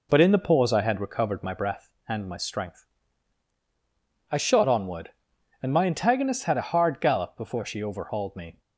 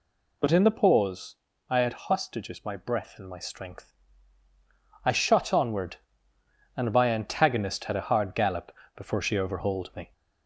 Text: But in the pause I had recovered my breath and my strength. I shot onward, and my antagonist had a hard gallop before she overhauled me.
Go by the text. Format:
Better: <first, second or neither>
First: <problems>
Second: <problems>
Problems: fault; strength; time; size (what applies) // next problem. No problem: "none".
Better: first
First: none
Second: pauses between "pause" and "I"; slight; at 1.3 s; 0.34 s long // says "hostages" for "recovered"; at 1.9 s // pauses between "gallop" and "before"; slight; at 8.6 s; 0.26 s long